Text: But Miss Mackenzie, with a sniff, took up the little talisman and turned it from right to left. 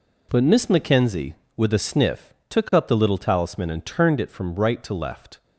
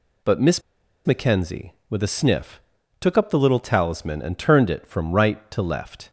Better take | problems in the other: first | pauses between "Miss" and "Mackenzie"; at 0.6 s; 0.44 s long

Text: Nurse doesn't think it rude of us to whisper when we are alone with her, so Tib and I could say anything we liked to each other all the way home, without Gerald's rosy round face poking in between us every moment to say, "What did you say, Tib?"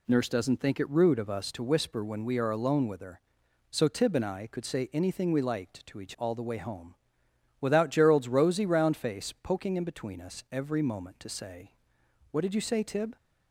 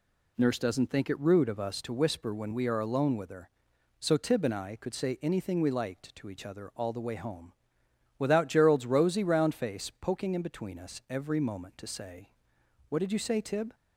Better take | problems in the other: second | skips "other"; at 6.1 s

